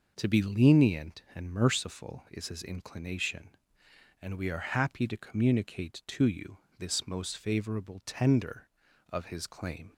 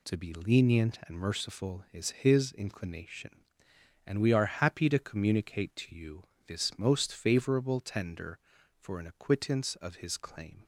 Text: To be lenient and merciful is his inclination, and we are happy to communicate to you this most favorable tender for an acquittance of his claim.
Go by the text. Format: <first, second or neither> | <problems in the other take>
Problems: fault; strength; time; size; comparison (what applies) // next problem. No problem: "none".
second | pauses between "you" and "this"; slight; at 6.5 s; 0.20 s long; slight in the second // skips "for an acquittance"; at 8.8 s